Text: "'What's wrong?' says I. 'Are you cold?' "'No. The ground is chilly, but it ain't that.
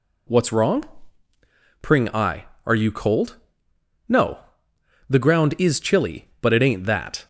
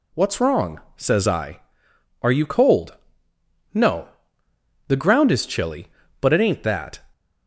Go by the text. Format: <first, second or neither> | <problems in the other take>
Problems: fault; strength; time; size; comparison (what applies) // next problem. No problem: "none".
second | says "pring" for "says"; at 1.7 s